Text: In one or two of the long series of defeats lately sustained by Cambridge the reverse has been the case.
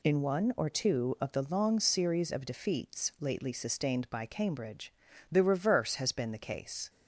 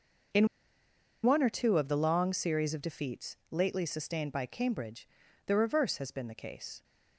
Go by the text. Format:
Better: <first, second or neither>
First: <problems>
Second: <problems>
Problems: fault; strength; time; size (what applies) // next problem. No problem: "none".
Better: first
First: pauses between "Cambridge" and "the"; slight; at 4.9 s; 0.36 s long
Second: pauses between "In" and "one"; noticeable; at 0.4 s; 0.76 s long // pauses between "Cambridge" and "the"; at 5.0 s; 0.38 s long